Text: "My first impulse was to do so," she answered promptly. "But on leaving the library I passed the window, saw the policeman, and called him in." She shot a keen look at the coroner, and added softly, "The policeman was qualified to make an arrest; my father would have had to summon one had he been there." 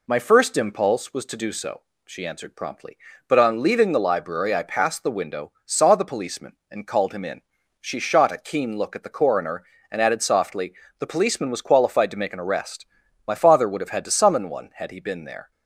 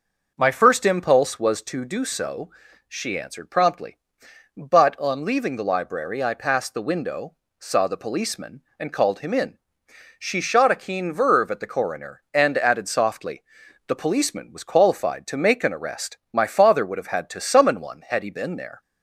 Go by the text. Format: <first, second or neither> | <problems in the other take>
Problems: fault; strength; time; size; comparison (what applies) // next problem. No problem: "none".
first | starts louder than the rest; noticeable; until 1.3 s; 6 dB // says "verve" for "look"; at 11.1 s